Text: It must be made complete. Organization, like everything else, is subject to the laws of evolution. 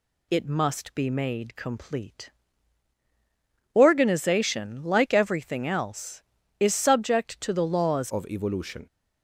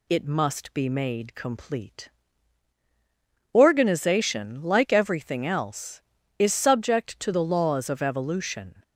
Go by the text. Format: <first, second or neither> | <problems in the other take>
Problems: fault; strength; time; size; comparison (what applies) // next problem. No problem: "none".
second | changes voice at "of"; from 8.1 s on; 0.7 s long